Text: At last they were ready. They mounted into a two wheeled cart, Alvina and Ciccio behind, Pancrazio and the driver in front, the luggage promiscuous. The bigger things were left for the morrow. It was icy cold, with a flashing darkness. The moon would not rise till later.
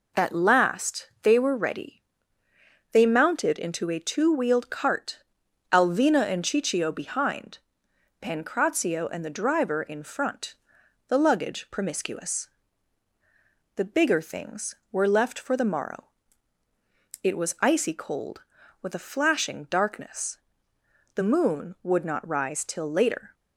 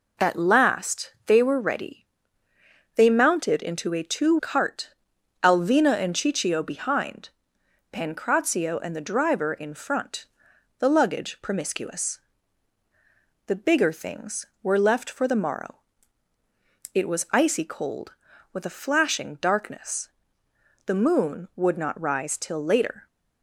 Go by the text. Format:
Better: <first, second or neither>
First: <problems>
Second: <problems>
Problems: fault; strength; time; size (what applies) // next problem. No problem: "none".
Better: first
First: none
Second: skips "wheeled"; at 4.3 s